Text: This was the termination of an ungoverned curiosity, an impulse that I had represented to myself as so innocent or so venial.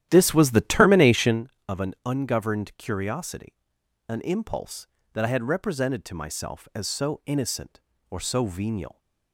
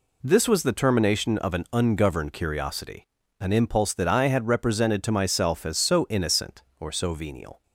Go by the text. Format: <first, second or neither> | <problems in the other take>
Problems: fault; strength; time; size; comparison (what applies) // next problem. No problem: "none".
second | starts louder than the rest; strong; until 1.4 s; 12 dB